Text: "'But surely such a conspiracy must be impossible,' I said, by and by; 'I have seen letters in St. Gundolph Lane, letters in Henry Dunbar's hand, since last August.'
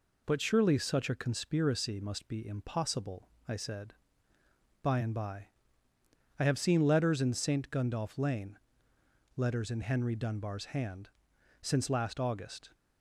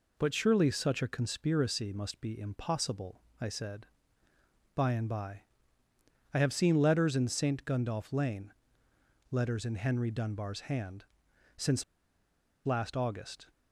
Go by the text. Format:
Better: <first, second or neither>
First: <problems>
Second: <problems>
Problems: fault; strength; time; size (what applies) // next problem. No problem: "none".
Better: first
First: none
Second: pauses between "since" and "last"; noticeable; at 11.8 s; 0.82 s long